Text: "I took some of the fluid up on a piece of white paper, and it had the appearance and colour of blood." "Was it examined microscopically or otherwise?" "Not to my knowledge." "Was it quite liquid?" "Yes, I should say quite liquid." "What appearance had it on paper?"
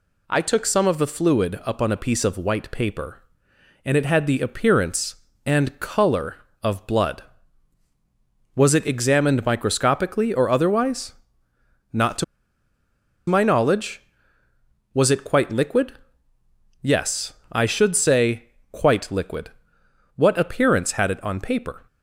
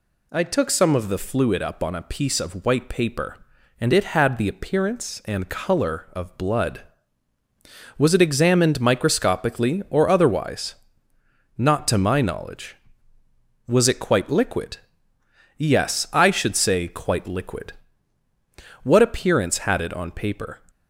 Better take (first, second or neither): second